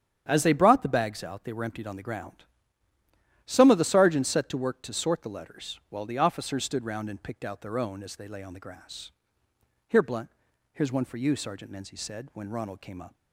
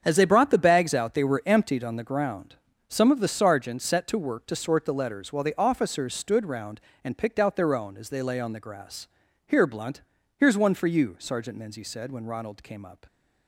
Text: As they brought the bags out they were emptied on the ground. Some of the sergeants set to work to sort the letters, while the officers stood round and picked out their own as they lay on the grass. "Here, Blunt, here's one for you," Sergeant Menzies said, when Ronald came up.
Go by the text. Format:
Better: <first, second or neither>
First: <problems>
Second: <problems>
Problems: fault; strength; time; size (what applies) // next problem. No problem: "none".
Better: neither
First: starts louder than the rest; strong; until 1.2 s; 9 dB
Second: starts louder than the rest; strong; until 1.0 s; 7.5 dB